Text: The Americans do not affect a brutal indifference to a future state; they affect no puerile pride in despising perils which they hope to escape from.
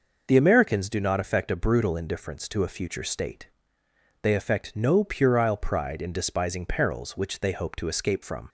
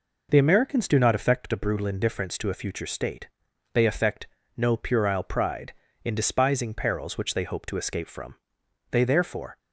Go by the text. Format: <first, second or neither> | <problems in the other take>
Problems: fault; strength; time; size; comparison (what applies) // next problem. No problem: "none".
first | pauses between "affect" and "no"; slight; at 4.2 s; 0.28 s long // goes on to say "They therefore"; noticeable; from 8.9 s on; 0.66 s long